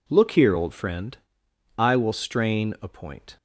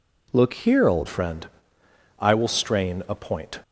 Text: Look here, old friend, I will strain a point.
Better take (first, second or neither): first